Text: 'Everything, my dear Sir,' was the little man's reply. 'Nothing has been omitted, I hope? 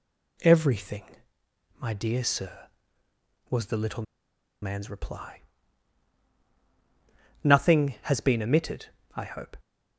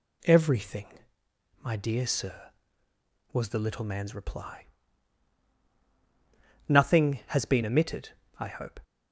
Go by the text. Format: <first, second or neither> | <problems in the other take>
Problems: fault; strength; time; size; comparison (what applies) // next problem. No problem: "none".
second | pauses between "little" and "man's"; noticeable; at 4.0 s; 0.58 s long